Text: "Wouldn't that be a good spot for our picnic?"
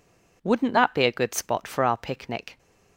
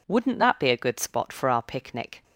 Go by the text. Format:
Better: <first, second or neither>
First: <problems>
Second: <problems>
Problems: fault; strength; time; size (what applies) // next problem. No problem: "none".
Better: neither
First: none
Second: none